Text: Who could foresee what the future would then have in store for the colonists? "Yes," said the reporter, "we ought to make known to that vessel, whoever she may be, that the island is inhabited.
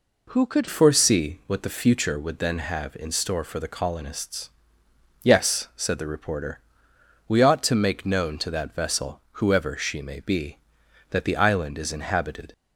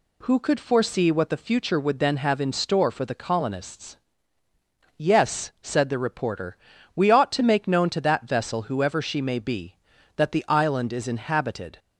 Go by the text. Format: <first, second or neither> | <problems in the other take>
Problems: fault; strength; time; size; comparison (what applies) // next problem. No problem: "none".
second | changes voice at "foresee"; from 0.6 s on; 11.9 s long